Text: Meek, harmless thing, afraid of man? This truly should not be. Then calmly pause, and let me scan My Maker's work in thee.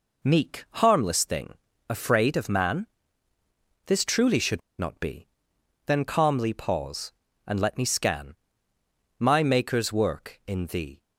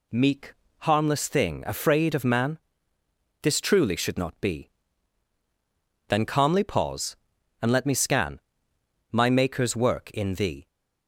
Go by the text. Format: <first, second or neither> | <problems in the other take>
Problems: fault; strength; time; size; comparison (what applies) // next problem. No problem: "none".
second | pauses between "should" and "not"; slight; at 4.6 s; 0.19 s long // pauses between "scan" and "My"; noticeable; at 8.3 s; 0.82 s long; noticeable in the second